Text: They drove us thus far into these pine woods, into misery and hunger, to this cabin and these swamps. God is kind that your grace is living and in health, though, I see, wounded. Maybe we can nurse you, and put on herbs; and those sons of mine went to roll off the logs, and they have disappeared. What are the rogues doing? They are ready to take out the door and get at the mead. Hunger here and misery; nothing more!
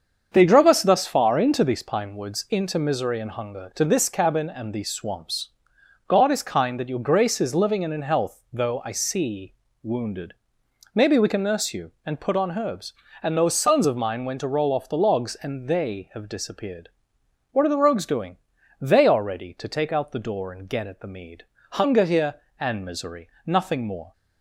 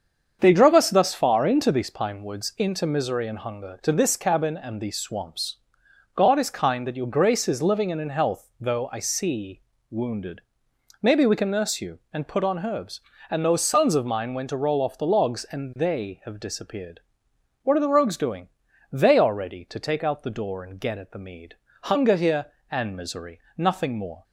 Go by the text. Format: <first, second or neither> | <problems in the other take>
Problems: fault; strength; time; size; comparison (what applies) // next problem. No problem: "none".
neither | starts louder than the rest; strong; the same in both